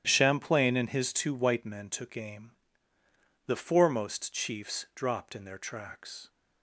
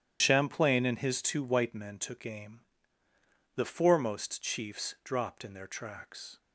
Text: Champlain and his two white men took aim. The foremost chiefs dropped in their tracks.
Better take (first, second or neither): first